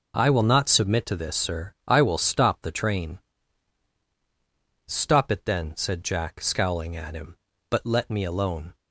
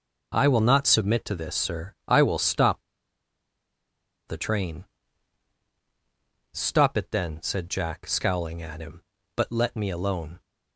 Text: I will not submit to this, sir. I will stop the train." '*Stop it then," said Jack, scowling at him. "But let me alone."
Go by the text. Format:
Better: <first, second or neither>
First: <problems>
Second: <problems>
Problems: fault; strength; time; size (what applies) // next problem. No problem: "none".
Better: first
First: none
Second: pauses between "stop" and "the"; strong; at 2.8 s; 1.4 s long